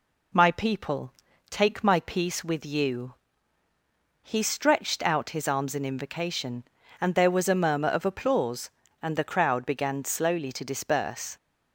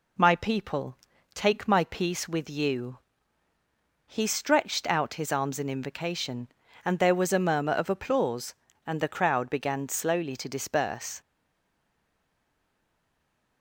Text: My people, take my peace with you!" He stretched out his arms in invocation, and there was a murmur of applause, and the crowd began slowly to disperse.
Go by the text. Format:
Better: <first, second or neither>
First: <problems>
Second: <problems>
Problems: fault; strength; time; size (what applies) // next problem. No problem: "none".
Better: first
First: none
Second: stays silent after the last word; from 11.2 s on; 2.4 s long